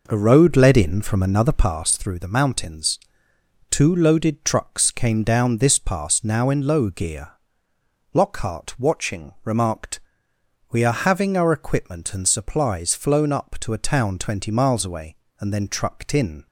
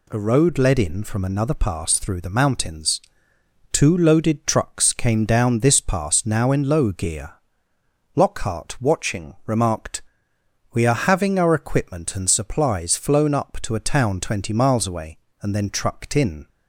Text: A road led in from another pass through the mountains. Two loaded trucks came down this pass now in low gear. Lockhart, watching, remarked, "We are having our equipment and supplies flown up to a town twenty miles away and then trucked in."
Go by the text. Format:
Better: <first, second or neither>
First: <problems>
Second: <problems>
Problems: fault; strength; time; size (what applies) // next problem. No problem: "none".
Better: second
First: starts louder than the rest; noticeable; until 1.9 s; 4.5 dB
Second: none